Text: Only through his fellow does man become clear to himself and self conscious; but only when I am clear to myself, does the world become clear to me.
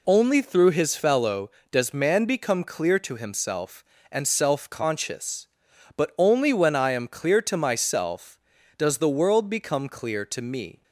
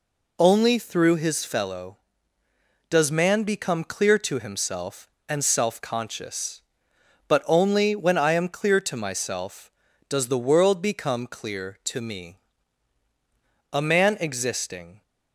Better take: first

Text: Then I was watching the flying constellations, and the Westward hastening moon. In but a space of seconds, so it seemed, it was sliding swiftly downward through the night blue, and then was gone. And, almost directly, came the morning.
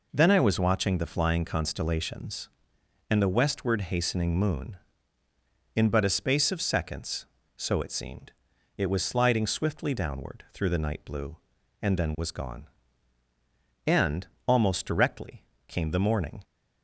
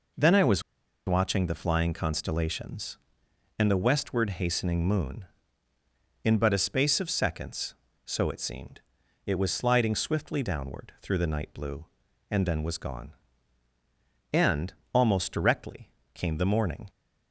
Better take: first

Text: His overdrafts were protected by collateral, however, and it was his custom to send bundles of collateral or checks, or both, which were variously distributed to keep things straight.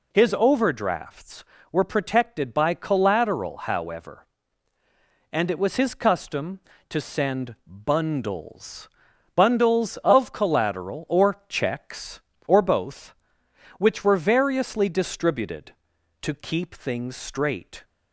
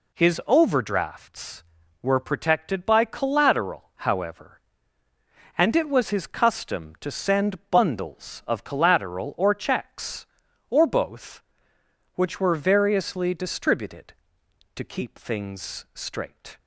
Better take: second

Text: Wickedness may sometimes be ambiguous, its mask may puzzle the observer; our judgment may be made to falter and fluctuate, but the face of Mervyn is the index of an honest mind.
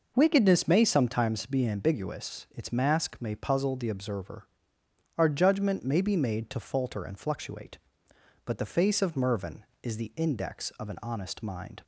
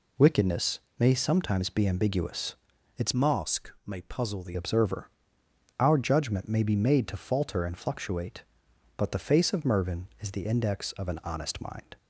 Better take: first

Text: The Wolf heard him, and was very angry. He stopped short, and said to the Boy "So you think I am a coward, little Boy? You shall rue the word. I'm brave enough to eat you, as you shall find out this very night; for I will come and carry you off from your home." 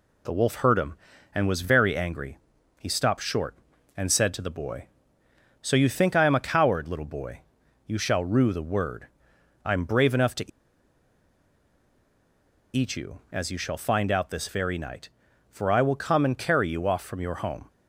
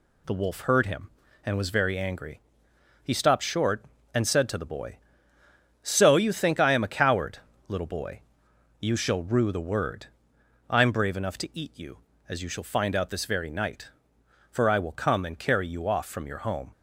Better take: second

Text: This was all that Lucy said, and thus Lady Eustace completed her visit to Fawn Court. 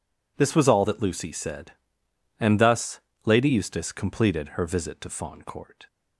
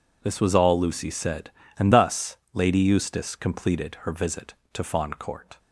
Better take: first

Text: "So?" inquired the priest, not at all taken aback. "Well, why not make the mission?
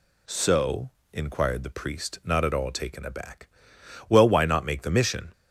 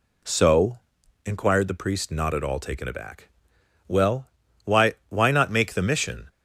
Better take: first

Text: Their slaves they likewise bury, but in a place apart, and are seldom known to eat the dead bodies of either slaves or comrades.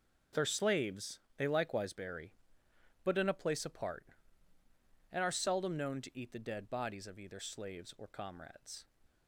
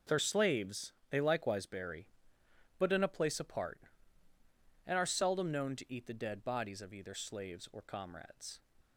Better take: neither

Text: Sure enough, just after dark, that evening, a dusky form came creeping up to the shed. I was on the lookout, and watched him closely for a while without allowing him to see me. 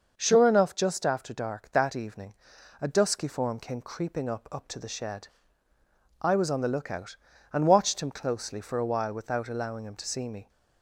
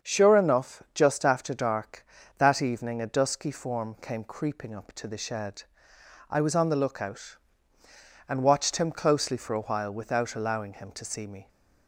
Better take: second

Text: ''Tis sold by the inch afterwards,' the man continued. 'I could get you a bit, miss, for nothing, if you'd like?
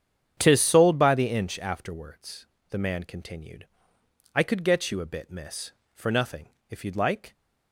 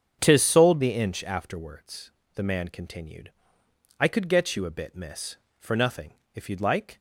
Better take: first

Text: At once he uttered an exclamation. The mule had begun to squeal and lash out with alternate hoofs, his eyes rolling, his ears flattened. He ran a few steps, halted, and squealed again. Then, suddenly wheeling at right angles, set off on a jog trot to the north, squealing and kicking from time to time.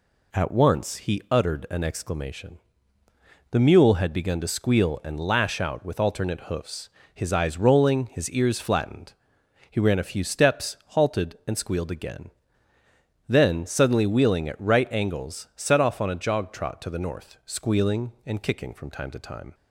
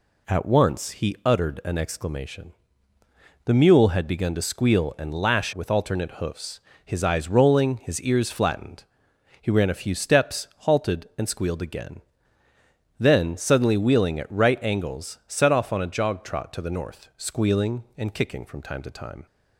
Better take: first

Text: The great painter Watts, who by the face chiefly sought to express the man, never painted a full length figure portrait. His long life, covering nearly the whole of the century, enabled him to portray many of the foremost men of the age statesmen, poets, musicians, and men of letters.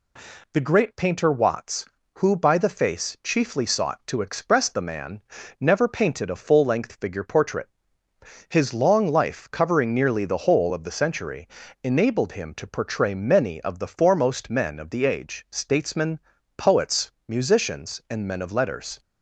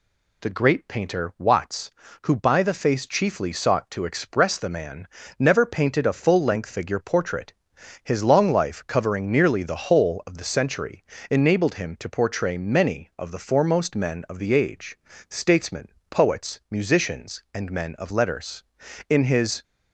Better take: first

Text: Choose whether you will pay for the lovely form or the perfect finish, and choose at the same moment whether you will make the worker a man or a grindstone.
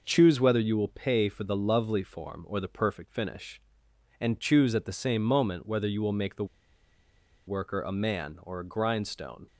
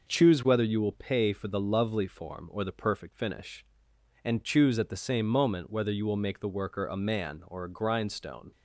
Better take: second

